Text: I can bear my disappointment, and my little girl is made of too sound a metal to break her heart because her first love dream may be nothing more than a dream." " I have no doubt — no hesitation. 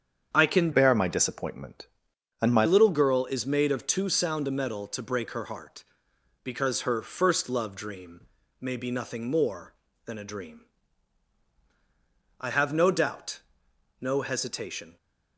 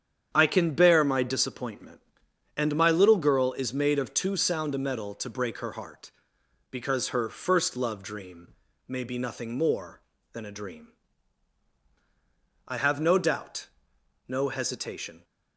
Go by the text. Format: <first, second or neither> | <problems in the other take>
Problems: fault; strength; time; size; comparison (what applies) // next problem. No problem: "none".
second | starts louder than the rest; strong; until 1.3 s; 8 dB; strong in the second // changes voice from "bear" to "my"; from 0.7 to 2.6 s; 1.9 s long // pauses between "dream" and "may"; at 8.2 s; 0.40 s long; also in the second